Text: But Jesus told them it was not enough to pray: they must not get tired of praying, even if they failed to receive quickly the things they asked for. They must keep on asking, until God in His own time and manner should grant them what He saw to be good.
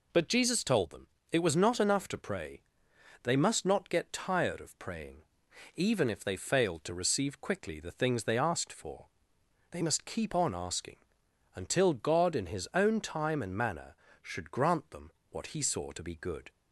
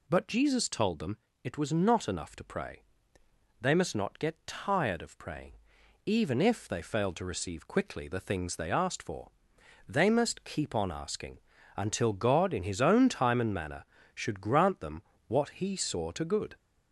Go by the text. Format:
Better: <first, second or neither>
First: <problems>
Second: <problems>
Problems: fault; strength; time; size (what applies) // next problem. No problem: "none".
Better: first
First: pauses between "them" and "it"; slight; at 1.0 s; 0.24 s long // pauses between "them" and "what"; slight; at 15.1 s; 0.18 s long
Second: pauses between "them" and "it"; slight; at 1.1 s; 0.26 s long // pauses between "them" and "what"; slight; at 15.0 s; 0.26 s long // skips "be"; at 16.2 s